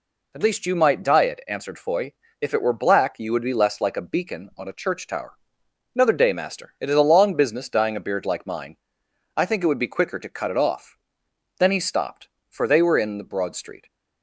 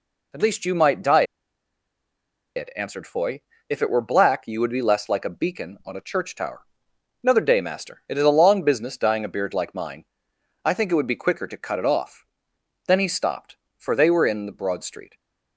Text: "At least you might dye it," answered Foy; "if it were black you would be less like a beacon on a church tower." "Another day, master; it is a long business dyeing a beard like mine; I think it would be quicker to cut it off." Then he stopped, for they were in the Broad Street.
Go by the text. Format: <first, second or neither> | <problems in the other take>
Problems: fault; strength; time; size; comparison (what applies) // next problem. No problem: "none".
first | pauses between "dye" and "it"; strong; at 1.2 s; 1.3 s long